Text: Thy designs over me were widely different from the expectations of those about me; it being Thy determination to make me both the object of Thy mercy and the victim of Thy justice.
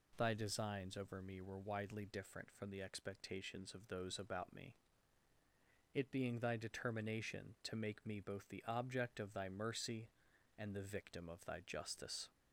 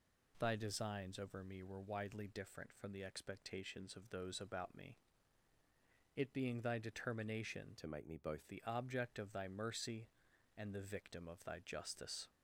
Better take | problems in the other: first | changes voice from "to" to "both"; from 7.7 to 8.4 s; 0.7 s long

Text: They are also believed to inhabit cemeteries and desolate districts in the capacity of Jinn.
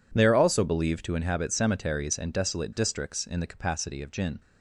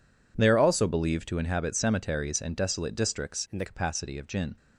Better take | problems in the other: first | changes voice from "in" to "the"; from 3.5 to 3.6 s; 0.1 s long

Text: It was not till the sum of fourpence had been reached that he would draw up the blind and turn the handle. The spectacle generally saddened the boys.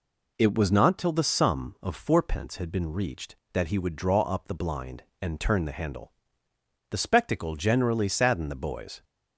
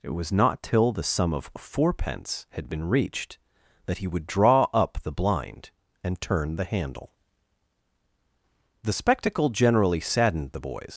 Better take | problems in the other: first | leaves "boys" unfinished; at 10.9 s; 110 ms

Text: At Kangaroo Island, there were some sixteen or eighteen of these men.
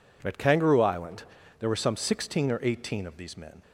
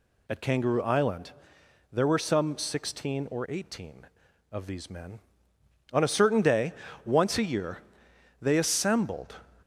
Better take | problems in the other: first | goes on to say "On a certain day once a year they assembled"; strong; from 5.9 s on; 3.4 s long

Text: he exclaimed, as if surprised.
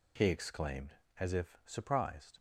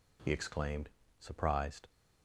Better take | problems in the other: first | skips "as if"; at 1.0 s

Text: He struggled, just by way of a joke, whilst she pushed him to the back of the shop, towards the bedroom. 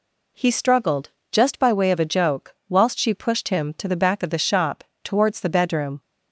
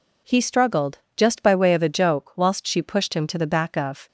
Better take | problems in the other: first | stops before "the shop towards the bedroom"; at 4.0 s

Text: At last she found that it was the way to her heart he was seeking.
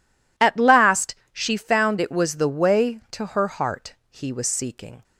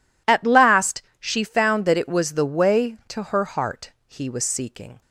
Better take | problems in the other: second | pauses between "last" and "she"; slight; at 1.1 s; 0.18 s long; slight in the second // skips "that"; at 1.9 s // pauses between "heart" and "he"; slight; at 3.9 s; 0.16 s long; slight in the second

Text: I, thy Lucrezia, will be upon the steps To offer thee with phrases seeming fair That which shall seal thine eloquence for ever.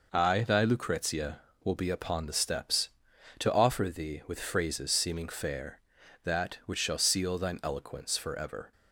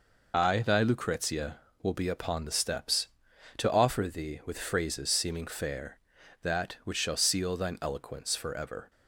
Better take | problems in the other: first | loses the start of "I"; at 0.3 s; 40 ms

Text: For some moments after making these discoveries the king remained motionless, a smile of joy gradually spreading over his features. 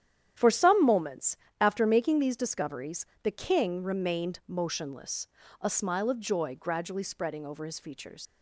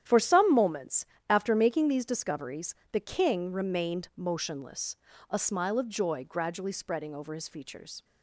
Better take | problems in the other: second | starts louder than the rest; strong; until 1.6 s; 10 dB; strong in the second // pauses between "moments" and "after"; slight; at 1.3 s; 0.24 s long; slight in the second // pauses between "discoveries" and "the"; slight; at 3.0 s; 0.16 s long; slight in the second // leaves "features" unfinished; at 8.2 s; 100 ms

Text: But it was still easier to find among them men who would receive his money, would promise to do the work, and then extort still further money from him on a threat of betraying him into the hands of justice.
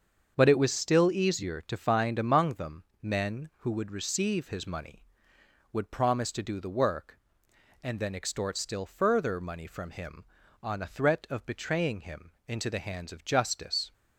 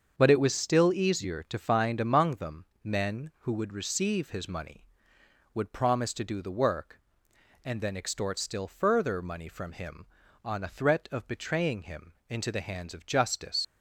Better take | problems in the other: first | starts louder than the rest; until 1.1 s; 7 dB; also in the first // pauses between "them" and "men"; slight; at 2.6 s; 0.18 s long; slight in the first // pauses between "him" and "into"; slight; at 12.1 s; 0.16 s long; slight in the first // leaves "justice" unfinished; at 13.6 s; 90 ms

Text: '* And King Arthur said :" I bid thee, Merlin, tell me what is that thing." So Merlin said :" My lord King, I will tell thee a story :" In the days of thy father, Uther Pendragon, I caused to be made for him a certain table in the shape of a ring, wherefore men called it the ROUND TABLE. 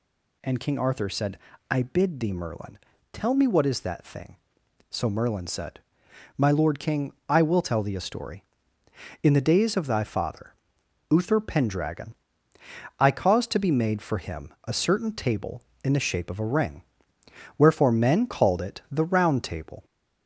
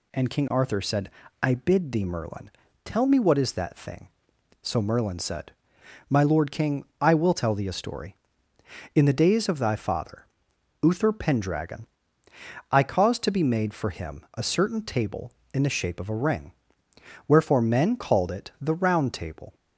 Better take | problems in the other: second | gets louder; noticeable; throughout; 4.5 dB

